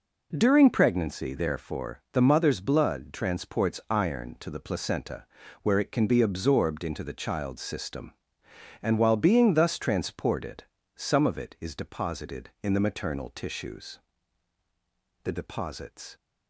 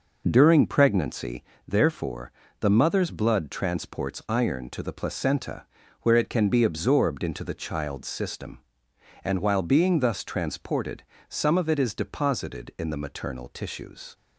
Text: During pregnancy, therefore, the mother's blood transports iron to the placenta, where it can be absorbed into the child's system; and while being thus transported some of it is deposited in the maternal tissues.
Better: second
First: pauses between "transported" and "some"; slight; at 10.6 s; 0.32 s long // goes on to say "The deposits"; noticeable; from 15.2 s on; 0.92 s long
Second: pauses between "transported" and "some"; slight; at 11.0 s; 0.26 s long

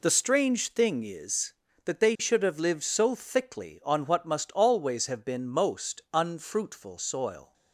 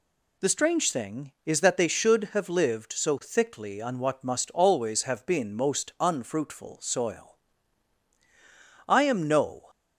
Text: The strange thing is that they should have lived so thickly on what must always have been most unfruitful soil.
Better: first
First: none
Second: goes on to say "I am no"; noticeable; from 8.8 s on; 0.80 s long

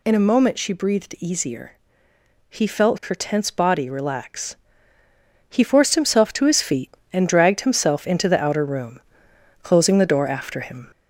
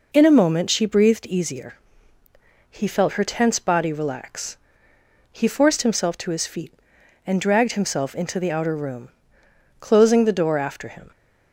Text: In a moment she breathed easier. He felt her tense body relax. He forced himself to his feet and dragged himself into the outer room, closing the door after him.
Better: second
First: gets louder; throughout; 3.5 dB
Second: none

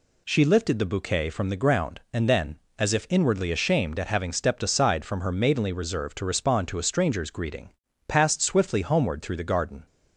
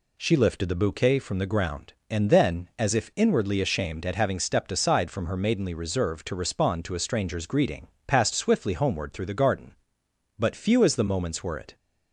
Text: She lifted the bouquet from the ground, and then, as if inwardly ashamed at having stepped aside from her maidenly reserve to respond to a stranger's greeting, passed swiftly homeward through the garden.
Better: first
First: none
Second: goes on to say "But few as the moments were it"; from 10.3 s on; 1.3 s long

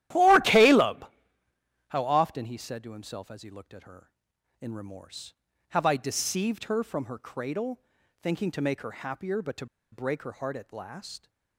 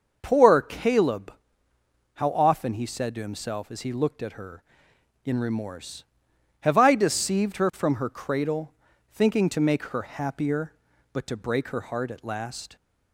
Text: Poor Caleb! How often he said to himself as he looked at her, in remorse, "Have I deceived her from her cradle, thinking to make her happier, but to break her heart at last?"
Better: second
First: starts louder than the rest; strong; until 1.9 s; 13.5 dB // pauses between "to" and "break"; slight; at 9.6 s; 0.26 s long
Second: starts louder than the rest; noticeable; until 1.2 s; 6 dB

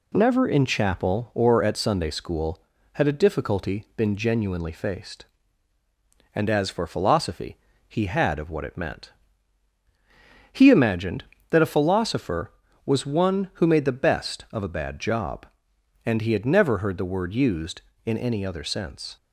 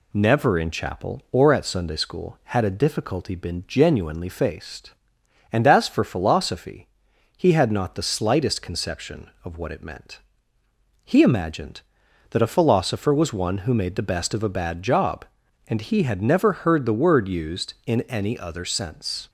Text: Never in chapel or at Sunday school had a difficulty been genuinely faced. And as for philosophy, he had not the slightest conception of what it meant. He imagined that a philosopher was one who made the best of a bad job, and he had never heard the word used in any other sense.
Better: second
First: skips "not the slightest conception"; at 8.3 s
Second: none

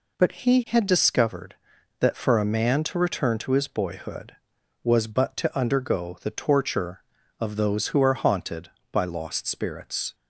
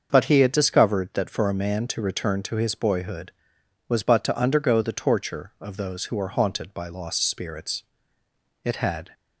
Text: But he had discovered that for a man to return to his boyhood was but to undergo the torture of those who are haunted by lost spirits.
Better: first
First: none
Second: starts louder than the rest; until 1.1 s; 6.5 dB // goes on to say "It had"; slight; from 8.6 s on; 0.46 s long

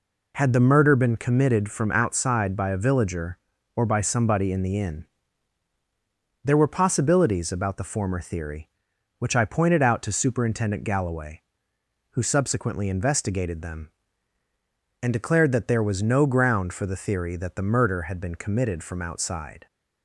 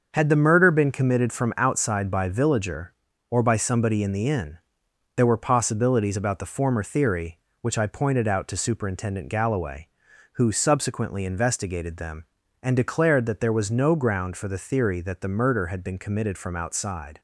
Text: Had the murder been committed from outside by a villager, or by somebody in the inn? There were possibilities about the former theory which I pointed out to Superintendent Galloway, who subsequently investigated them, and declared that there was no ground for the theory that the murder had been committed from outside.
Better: first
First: none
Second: starts louder than the rest; until 1.1 s; 6.5 dB // skips "a"; at 2.2 s

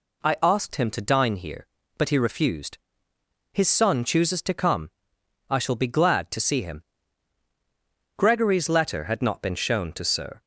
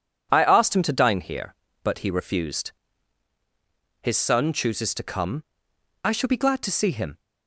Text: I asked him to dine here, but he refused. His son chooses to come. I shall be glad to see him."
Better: second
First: goes on to say "Gregory's letter had not been shown to Sir"; strong; from 8.1 s on; 2.2 s long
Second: none

